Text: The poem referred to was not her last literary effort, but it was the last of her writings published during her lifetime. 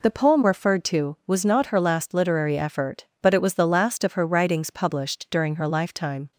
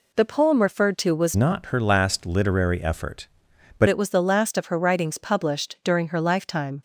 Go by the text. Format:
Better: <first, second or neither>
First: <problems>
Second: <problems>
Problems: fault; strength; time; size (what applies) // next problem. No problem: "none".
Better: first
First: none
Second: changes voice from "not" to "but"; from 1.3 to 3.8 s; 2.5 s long